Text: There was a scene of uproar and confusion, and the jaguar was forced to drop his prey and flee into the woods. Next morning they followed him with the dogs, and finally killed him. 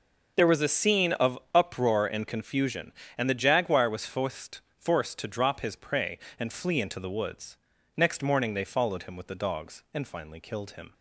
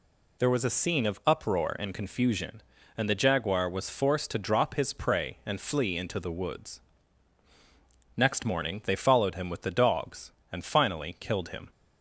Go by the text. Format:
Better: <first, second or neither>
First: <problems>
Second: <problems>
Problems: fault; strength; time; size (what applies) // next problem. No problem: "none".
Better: second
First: says "forced" twice; at 4.7 s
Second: none